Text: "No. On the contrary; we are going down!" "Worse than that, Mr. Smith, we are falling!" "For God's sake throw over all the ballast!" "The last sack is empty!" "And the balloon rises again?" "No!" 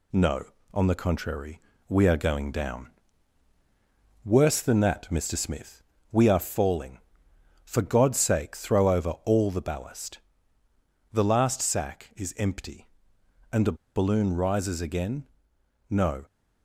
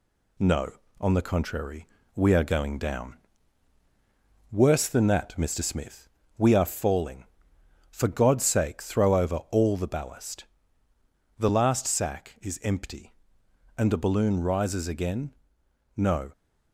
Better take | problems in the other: second | pauses between "the" and "balloon"; slight; at 13.7 s; 0.21 s long

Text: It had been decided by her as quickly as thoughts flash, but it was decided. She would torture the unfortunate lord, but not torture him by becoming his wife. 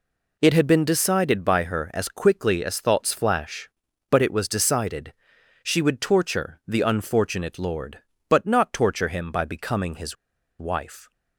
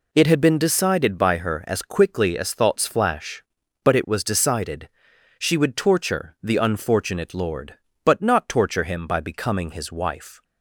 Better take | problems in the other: second | pauses between "his" and "wife"; at 10.1 s; 0.43 s long

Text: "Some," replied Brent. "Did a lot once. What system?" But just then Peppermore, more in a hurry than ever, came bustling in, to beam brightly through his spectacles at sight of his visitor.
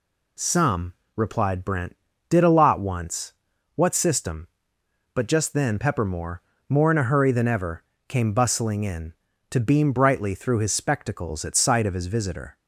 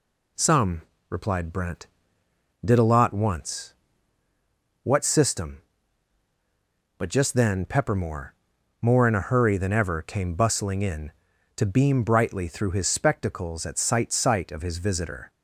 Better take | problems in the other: first | says "sight" twice; at 14.1 s

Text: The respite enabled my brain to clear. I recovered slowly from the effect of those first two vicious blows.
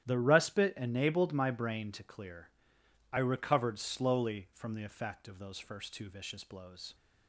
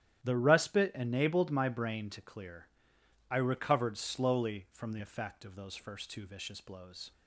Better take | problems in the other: neither | starts louder than the rest; strong; the same in both

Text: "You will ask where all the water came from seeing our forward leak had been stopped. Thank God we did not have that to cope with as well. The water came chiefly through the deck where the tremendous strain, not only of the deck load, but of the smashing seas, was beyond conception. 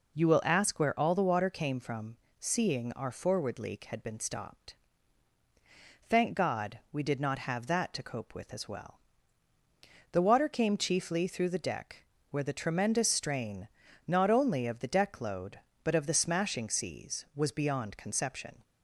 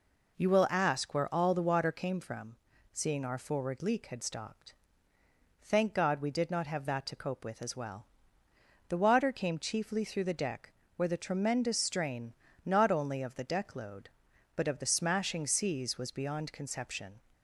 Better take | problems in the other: first | pauses between "from" and "seeing"; slight; at 2.5 s; 0.36 s long; slight in the first // skips "been"; at 4.2 s // pauses between "deck" and "where"; slight; at 10.7 s; 0.24 s long; slight in the first

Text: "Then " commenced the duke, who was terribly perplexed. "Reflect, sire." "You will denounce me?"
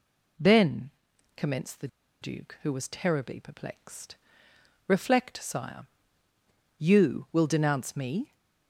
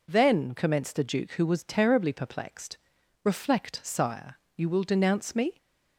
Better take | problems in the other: second | pauses between "the" and "duke"; slight; at 1.8 s; 0.35 s long

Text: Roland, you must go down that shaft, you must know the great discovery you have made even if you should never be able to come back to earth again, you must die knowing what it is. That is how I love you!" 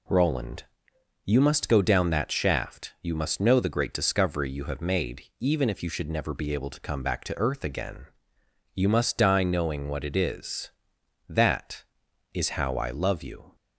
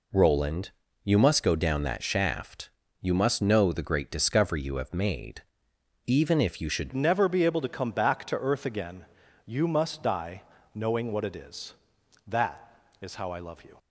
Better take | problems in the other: first | pauses between "made" and "even"; noticeable; at 5.4 s; 0.66 s long; slight in the first // changes voice at "never"; from 6.9 s on; 6.8 s long // pauses between "die" and "knowing"; slight; at 10.4 s; 0.32 s long

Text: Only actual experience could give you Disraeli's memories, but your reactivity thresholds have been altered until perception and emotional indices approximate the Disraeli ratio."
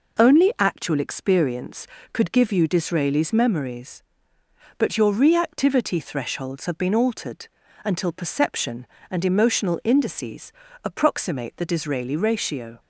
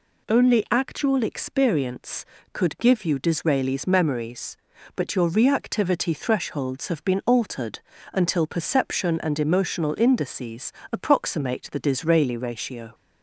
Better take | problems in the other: neither | pauses between "altered" and "until"; slight; the same in both // pauses between "indices" and "approximate"; slight; the same in both

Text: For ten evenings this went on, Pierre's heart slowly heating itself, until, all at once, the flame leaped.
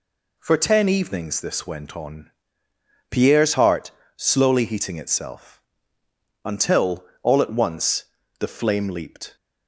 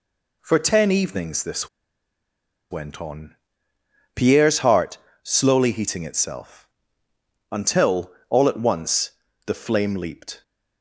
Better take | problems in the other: first | pauses between "this" and "went"; at 1.6 s; 1.0 s long // pauses between "heart" and "slowly"; slight; at 4.9 s; 0.26 s long; slight in the first

